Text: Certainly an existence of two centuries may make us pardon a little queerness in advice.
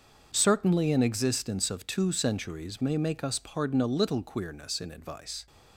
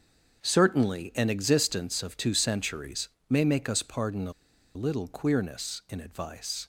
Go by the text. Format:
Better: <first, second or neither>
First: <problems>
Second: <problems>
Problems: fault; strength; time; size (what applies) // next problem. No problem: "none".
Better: first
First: starts louder than the rest; until 1.3 s; 7 dB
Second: starts louder than the rest; until 1.4 s; 6.5 dB // pauses between "centuries" and "may"; slight; at 3.0 s; 0.18 s long // pauses between "a" and "little"; at 4.3 s; 0.43 s long